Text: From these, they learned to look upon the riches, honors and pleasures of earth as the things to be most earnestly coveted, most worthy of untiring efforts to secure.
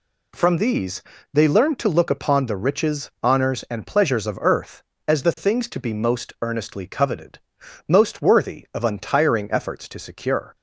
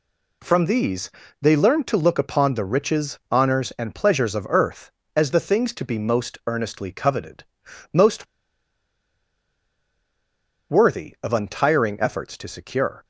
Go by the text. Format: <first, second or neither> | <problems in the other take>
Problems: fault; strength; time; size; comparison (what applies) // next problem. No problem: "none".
first | pauses between "most" and "worthy"; strong; at 8.2 s; 2.4 s long